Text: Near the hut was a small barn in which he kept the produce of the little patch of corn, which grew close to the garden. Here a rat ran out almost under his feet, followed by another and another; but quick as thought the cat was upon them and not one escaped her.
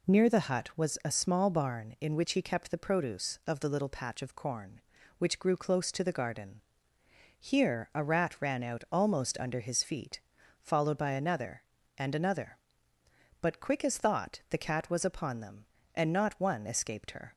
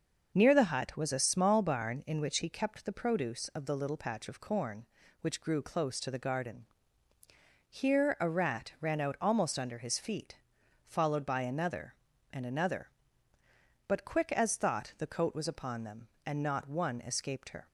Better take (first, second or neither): first